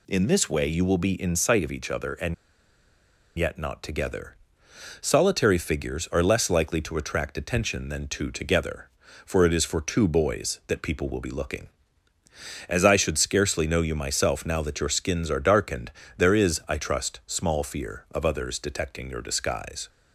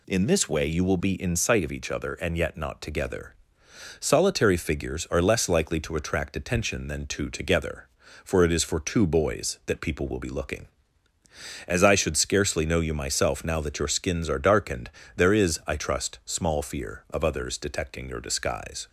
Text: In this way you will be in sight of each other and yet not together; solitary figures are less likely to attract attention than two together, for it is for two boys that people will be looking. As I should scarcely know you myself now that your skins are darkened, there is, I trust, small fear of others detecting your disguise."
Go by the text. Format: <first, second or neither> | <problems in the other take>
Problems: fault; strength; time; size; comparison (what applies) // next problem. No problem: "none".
second | pauses between "and" and "yet"; at 2.3 s; 1.0 s long